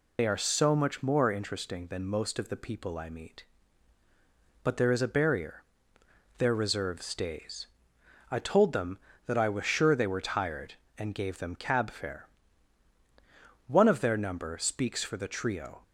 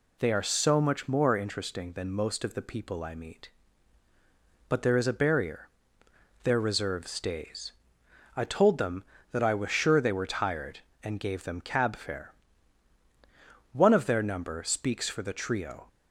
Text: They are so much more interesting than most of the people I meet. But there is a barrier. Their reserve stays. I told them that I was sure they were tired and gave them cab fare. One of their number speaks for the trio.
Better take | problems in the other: second | loses the start of "They"; at 0.1 s; 45 ms

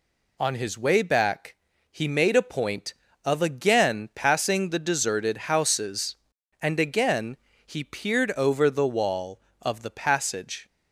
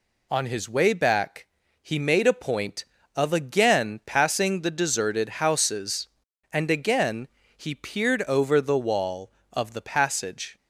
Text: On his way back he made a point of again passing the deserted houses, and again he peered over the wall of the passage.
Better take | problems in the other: neither | pauses between "back" and "he"; slight; the same in both // pauses between "again" and "he"; slight; the same in both

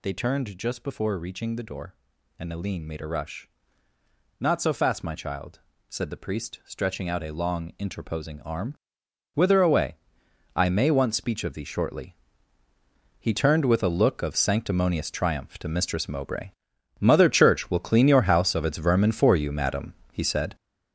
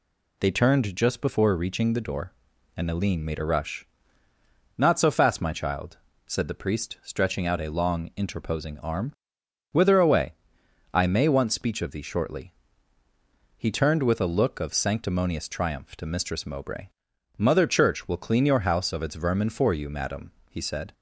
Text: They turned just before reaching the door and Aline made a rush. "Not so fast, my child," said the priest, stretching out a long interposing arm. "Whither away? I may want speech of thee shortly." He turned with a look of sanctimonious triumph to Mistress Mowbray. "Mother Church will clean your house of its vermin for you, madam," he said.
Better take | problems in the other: second | gets louder; strong; throughout; 8 dB

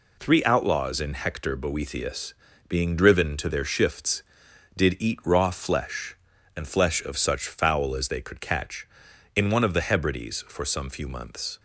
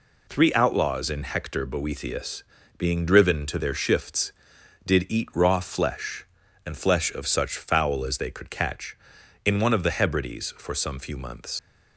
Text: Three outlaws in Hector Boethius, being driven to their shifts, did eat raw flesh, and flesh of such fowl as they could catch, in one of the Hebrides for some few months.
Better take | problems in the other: first | leaves "months" unfinished; at 11.5 s; 100 ms

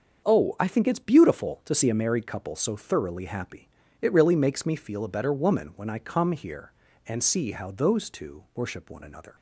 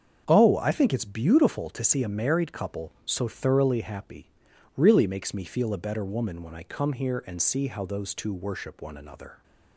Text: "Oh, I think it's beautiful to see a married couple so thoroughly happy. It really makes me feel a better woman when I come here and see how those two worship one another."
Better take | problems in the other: first | starts louder than the rest; until 1.2 s; 7 dB; also in the first // skips "It"; at 4.5 s

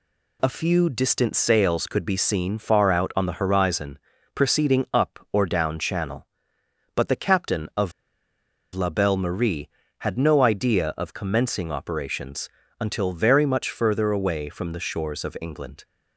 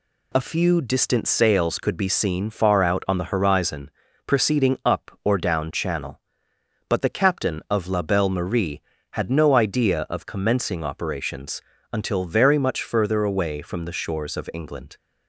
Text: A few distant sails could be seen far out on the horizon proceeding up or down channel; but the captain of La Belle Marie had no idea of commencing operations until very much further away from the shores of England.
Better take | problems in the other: second | pauses between "horizon" and "proceeding"; slight; at 3.9 s; 0.34 s long; slight in the second // pauses between "of" and "La"; noticeable; at 7.9 s; 0.82 s long // pauses between "operations" and "until"; slight; at 12.4 s; 0.30 s long; slight in the second

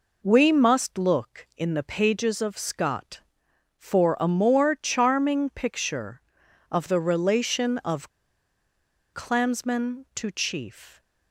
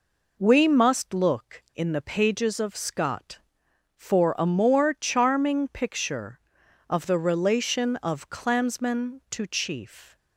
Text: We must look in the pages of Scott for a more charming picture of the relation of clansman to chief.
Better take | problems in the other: second | pauses between "of" and "clansman"; at 8.1 s; 1.0 s long

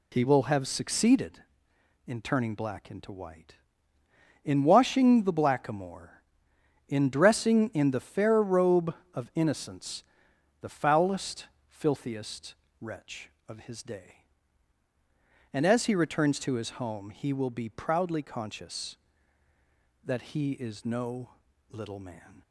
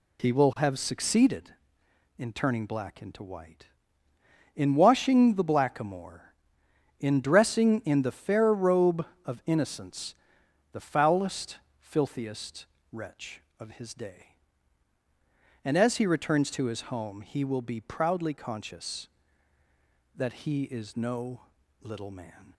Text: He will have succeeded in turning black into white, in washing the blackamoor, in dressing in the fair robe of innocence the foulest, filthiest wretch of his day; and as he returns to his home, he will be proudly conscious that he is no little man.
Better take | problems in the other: neither | pauses between "innocence" and "the"; noticeable; the same in both // pauses between "filthiest" and "wretch"; slight; the same in both // pauses between "no" and "little"; the same in both

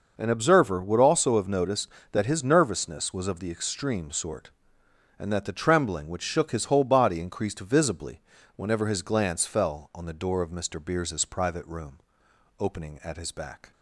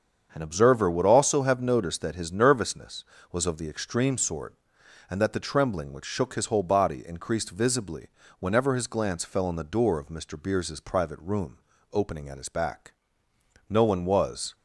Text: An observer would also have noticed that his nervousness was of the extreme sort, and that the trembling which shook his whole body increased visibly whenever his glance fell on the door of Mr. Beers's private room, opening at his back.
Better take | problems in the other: first | starts louder than the rest; until 1.3 s; 7 dB // pauses between "visibly" and "whenever"; slight; at 8.0 s; 0.32 s long; slight in the first // goes on to say "No one was"; noticeable; from 13.6 s on; 0.86 s long

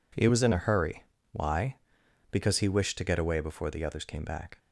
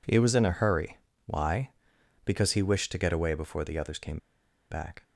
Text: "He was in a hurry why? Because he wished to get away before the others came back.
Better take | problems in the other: first | pauses between "hurry" and "why"; slight; at 0.9 s; 0.26 s long; slight in the first // pauses between "came" and "back"; noticeable; at 4.1 s; 0.52 s long

